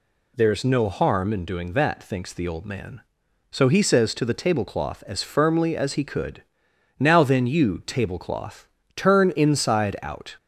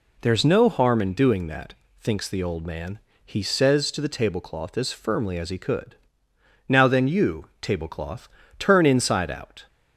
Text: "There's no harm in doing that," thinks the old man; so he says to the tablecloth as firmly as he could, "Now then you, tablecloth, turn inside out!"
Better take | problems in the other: first | skips "so"; at 3.1 s

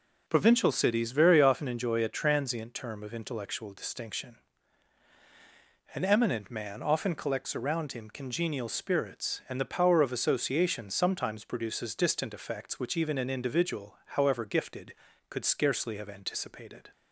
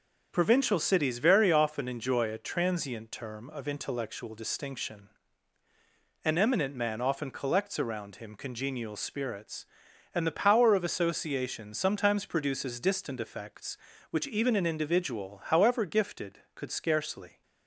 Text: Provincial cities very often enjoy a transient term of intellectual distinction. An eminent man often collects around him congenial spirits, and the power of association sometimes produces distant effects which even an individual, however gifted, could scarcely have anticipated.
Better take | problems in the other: first | starts louder than the rest; until 1.3 s; 6.5 dB // stops before "have anticipated"; at 17.4 s

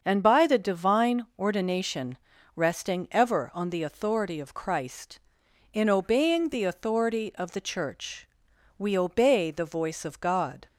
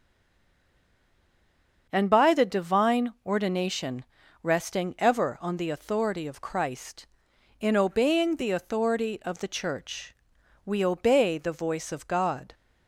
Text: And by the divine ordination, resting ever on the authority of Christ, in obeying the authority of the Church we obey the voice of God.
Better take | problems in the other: first | stays silent before the first word; noticeable; until 1.8 s; 1.8 s long // starts louder than the rest; until 2.9 s; 6.5 dB; also in the first // pauses between "Church" and "we"; noticeable; at 10.1 s; 0.52 s long; noticeable in the first

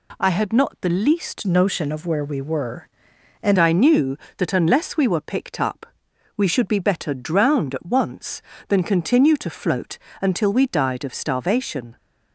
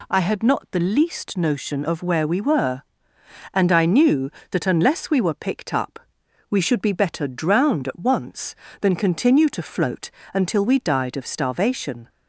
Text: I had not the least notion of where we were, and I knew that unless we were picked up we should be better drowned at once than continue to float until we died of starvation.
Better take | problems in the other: second | changes voice from "notion" to "and"; from 1.4 to 3.5 s; 2.1 s long // pauses between "up" and "we"; noticeable; at 5.8 s; 0.52 s long; noticeable in the second // pauses between "float" and "until"; slight; at 9.9 s; 0.24 s long; slight in the second

